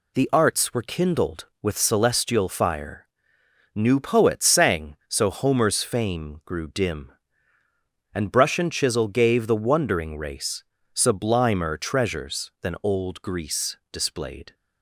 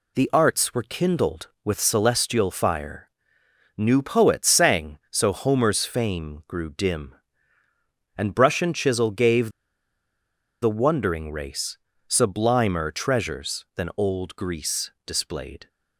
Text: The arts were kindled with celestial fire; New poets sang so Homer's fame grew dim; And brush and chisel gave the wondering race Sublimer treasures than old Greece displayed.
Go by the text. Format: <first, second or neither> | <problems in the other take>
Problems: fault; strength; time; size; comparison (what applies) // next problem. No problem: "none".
first | pauses between "gave" and "the"; at 9.5 s; 1.1 s long // pauses between "race" and "Sublimer"; slight; at 11.7 s; 0.32 s long; slight in the first